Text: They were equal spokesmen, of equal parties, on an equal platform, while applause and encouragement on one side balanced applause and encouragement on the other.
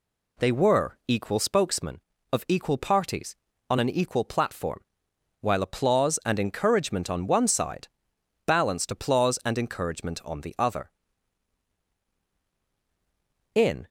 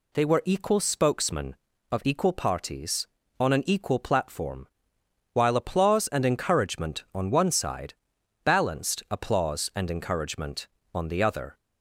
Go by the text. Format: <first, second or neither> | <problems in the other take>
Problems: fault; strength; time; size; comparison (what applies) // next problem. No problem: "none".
second | pauses between "side" and "balanced"; noticeable; at 7.8 s; 0.58 s long; noticeable in the second // goes on to say "In"; slight; from 13.5 s on; 0.32 s long